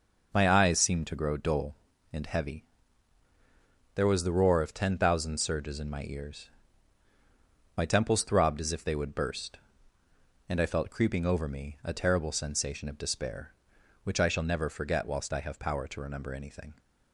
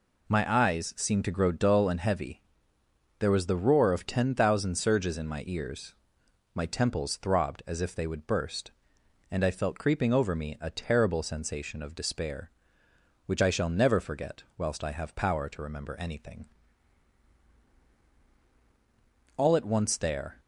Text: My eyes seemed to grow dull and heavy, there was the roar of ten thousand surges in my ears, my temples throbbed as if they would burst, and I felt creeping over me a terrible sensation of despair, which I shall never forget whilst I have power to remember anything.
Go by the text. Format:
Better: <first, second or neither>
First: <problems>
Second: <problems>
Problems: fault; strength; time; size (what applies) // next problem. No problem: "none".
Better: first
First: none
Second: goes on to say "All at once there"; noticeable; from 19.3 s on; 1.0 s long